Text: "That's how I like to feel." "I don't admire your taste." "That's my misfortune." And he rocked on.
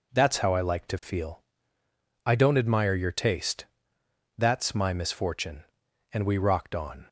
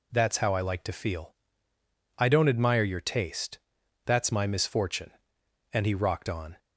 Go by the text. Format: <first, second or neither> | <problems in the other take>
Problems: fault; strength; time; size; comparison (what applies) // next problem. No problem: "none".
second | says "we" for "he"; at 6.2 s